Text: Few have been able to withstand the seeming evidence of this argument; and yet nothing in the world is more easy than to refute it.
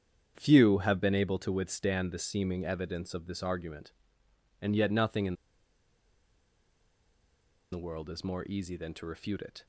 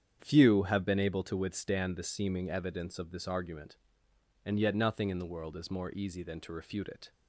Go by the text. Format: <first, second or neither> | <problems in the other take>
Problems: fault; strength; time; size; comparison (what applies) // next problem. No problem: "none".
second | starts louder than the rest; strong; until 1.3 s; 8.5 dB; strong in the second // pauses between "in" and "the"; strong; at 5.3 s; 2.3 s long